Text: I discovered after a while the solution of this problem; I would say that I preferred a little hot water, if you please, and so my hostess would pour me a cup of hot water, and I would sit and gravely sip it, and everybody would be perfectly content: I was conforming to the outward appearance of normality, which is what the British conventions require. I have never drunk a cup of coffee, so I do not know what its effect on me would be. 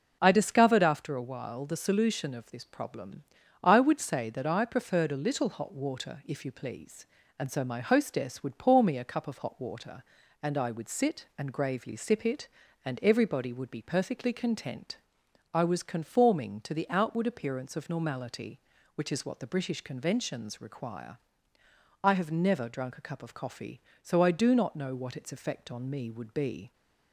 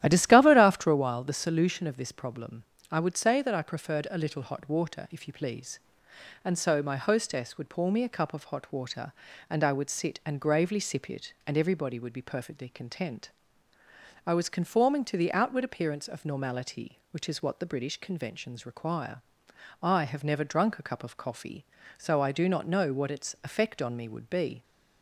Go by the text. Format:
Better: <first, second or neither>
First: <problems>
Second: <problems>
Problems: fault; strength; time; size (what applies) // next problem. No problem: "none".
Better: first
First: none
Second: starts louder than the rest; strong; until 1.0 s; 12.5 dB